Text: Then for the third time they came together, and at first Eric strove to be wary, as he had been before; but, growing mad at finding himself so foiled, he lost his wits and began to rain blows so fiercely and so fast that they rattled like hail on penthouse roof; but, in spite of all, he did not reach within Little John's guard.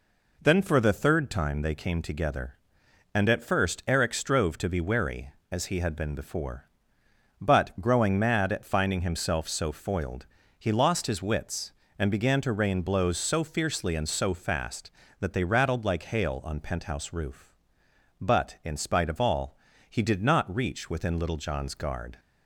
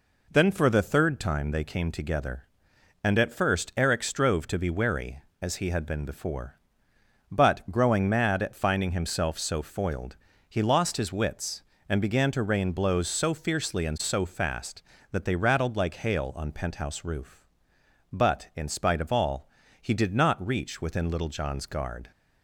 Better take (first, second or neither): neither